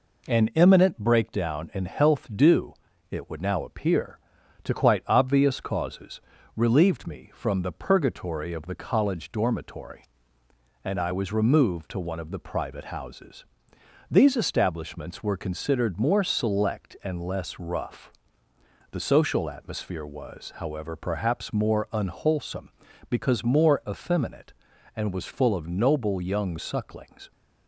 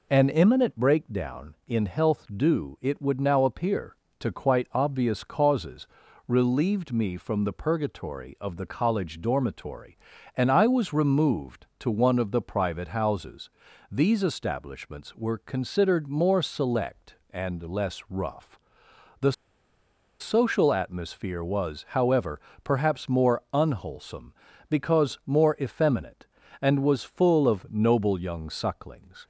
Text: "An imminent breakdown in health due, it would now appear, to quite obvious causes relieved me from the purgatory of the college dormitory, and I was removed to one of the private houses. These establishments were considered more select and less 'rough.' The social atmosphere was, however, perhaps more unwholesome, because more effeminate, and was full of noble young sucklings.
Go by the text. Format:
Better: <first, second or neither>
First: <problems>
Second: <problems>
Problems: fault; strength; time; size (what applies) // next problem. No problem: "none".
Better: first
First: pauses between "causes" and "relieved"; slight; at 6.2 s; 0.34 s long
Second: pauses between "causes" and "relieved"; at 5.8 s; 0.40 s long // pauses between "The" and "social"; noticeable; at 19.3 s; 0.87 s long